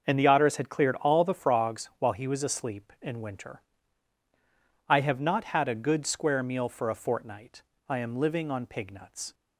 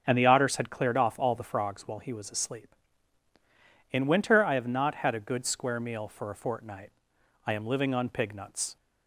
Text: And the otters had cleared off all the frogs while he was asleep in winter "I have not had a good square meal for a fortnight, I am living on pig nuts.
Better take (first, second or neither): second